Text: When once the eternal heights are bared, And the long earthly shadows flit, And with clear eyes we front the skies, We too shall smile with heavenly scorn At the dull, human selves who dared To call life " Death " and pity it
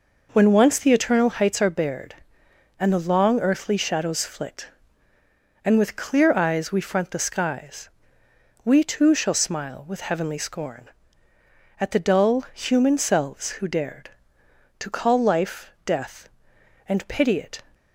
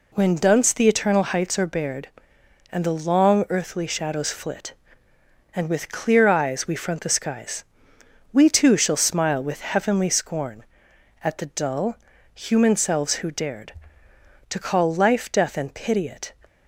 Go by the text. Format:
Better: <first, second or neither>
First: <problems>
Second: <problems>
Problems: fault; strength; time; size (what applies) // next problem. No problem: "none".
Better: first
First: none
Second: says "dunce" for "once"; at 0.3 s